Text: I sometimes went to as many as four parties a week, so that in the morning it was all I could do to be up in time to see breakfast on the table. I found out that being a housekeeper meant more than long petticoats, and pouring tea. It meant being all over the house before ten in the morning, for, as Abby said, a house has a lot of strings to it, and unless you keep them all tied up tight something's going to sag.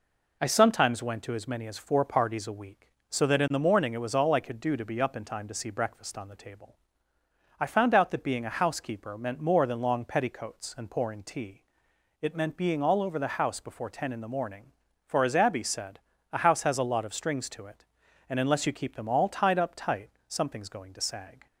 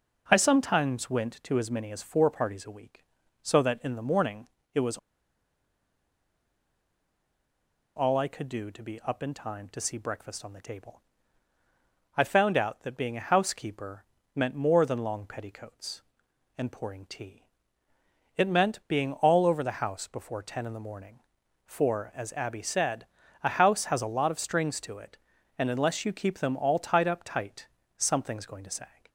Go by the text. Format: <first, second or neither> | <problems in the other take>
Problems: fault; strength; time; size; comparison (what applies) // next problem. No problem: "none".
first | pauses between "morning" and "it"; slight; at 4.4 s; 0.26 s long // pauses between "was" and "all"; strong; at 4.9 s; 2.9 s long // pauses between "housekeeper" and "meant"; slight; at 14.0 s; 0.32 s long // pauses between "tight" and "something's"; slight; at 27.6 s; 0.28 s long; slight in the first